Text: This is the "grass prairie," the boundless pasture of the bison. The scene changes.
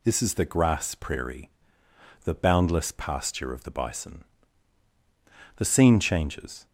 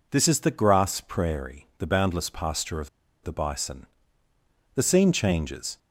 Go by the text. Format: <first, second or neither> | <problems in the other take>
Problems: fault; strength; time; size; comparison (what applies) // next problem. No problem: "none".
first | pauses between "of" and "the"; slight; at 2.8 s; 0.34 s long